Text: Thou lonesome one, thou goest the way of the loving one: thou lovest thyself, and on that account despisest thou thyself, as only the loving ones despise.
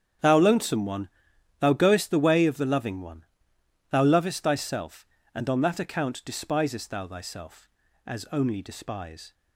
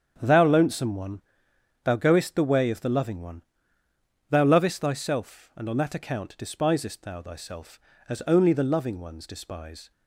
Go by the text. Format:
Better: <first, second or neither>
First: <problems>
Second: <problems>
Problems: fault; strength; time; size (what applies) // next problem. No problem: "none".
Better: second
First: starts louder than the rest; strong; until 1.7 s; 8.5 dB // skips "the loving ones"; at 8.6 s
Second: starts louder than the rest; strong; until 1.2 s; 8 dB